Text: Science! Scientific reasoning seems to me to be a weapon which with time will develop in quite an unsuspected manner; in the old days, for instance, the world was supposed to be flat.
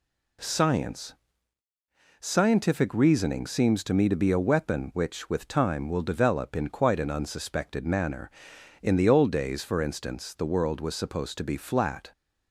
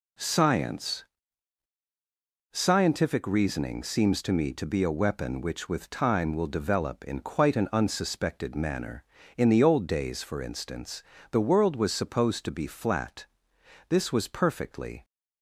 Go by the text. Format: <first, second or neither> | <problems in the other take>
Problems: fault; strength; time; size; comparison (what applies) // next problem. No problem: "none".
first | goes on to say "This was perfectly"; noticeable; from 13.9 s on; 1.1 s long